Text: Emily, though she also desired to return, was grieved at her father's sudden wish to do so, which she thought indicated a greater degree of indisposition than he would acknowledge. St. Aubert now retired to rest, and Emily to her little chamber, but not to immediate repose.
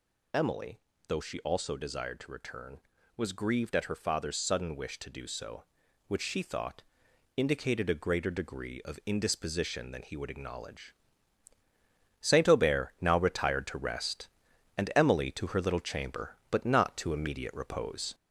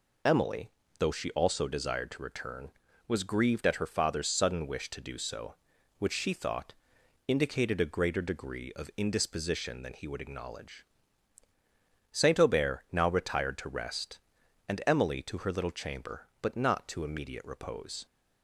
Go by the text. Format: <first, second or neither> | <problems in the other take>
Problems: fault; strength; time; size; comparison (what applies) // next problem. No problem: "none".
second | gets louder; noticeable; throughout; 4 dB // pauses between "thought" and "indicated"; noticeable; at 6.8 s; 0.54 s long; noticeable in the second